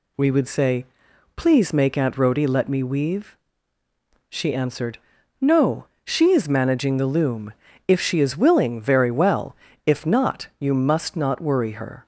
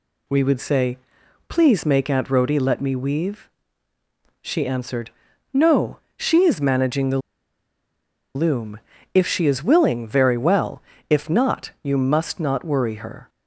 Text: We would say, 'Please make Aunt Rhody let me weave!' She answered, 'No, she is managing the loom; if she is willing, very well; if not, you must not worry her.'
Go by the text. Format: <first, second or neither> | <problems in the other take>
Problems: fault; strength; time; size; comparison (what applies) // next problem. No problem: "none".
first | pauses between "the" and "loom"; at 7.1 s; 1.1 s long